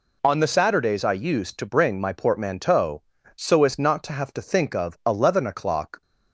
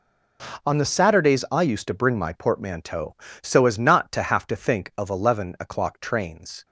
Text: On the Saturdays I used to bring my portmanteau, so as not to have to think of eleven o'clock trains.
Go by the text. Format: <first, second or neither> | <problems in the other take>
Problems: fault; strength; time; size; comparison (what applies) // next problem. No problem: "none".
second | stops before "trains"; at 6.0 s